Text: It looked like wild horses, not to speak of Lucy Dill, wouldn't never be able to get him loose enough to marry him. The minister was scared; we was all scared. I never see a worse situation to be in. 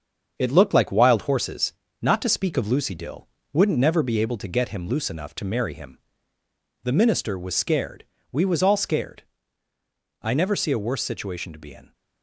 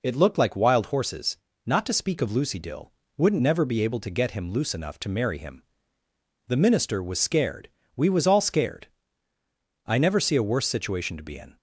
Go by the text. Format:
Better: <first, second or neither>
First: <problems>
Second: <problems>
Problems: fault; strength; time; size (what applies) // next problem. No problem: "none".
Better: second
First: gets quieter; noticeable; throughout; 5.5 dB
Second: none